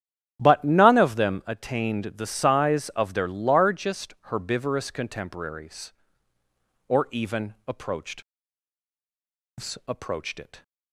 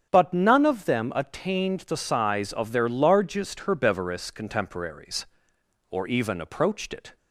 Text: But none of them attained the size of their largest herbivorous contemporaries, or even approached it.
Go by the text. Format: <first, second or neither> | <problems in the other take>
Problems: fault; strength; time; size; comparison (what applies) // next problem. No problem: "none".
second | starts louder than the rest; strong; until 1.4 s; 9.5 dB; strong in the second // says "approached" twice; at 9.8 s